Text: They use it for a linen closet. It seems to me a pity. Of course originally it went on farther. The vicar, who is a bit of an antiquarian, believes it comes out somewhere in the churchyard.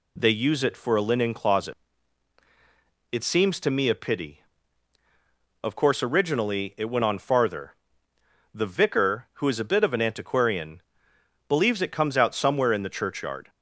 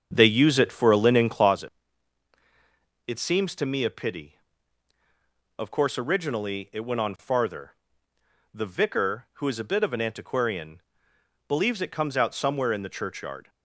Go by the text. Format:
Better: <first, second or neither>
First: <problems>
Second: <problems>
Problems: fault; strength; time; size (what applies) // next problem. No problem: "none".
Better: first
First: none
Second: starts louder than the rest; until 1.6 s; 7 dB